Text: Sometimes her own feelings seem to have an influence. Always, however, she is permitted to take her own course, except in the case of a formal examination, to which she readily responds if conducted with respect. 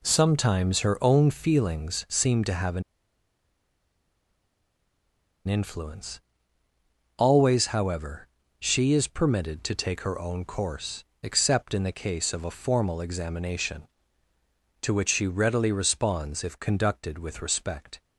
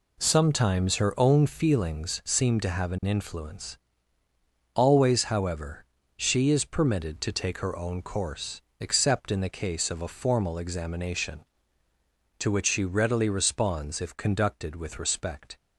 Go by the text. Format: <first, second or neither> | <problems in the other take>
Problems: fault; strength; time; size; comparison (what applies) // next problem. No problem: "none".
second | pauses between "an" and "influence"; strong; at 2.8 s; 2.6 s long